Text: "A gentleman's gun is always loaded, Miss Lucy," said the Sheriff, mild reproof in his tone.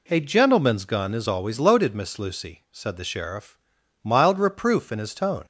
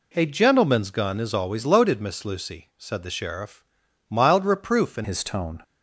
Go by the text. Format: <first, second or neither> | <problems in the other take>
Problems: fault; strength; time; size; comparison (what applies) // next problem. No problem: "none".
first | changes voice at "his"; from 5.0 s on; 0.6 s long